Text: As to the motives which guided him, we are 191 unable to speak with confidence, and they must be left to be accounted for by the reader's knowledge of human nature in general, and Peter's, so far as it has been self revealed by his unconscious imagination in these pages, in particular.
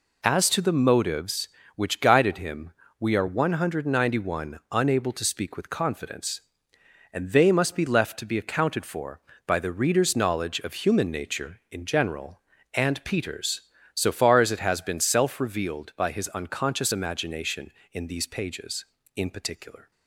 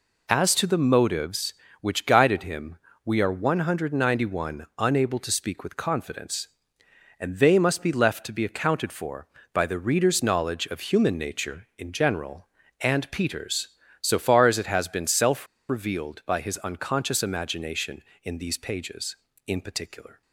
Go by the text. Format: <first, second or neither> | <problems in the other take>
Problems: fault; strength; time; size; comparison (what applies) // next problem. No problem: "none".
first | pauses between "self" and "revealed"; slight; at 15.4 s; 0.22 s long